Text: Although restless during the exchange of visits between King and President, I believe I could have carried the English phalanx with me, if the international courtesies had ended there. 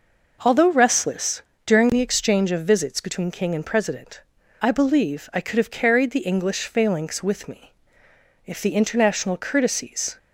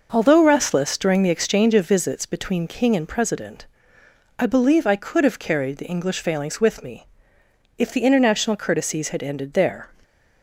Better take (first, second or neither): second